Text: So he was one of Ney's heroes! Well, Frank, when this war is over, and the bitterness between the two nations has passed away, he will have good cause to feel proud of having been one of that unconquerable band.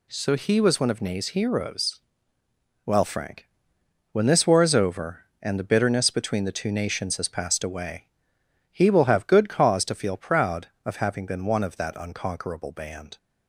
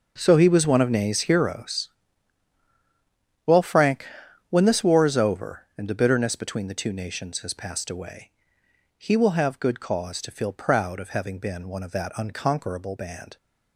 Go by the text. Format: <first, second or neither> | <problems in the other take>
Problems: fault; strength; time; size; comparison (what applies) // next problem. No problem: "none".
first | gets quieter; strong; throughout; 13 dB